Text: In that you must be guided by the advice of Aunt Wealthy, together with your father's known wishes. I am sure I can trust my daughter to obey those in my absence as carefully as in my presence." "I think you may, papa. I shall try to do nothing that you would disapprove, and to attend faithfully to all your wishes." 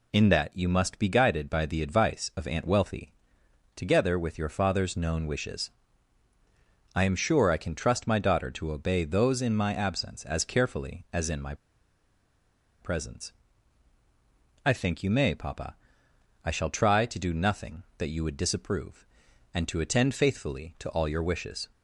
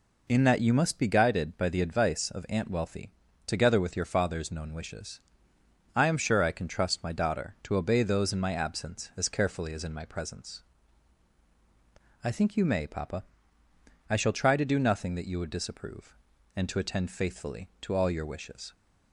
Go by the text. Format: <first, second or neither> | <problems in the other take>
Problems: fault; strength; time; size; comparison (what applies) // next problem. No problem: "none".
second | pauses between "my" and "presence"; strong; at 11.5 s; 1.2 s long